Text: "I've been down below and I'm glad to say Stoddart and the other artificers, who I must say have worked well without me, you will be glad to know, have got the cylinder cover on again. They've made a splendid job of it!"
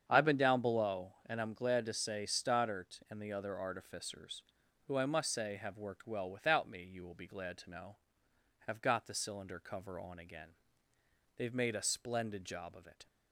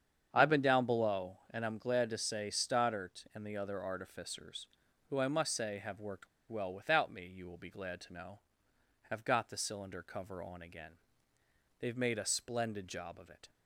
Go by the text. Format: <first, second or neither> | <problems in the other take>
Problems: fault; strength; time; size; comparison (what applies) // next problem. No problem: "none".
first | starts louder than the rest; strong; until 1.3 s; 8 dB; strong in the first // pauses between "worked" and "well"; slight; at 6.2 s; 0.21 s long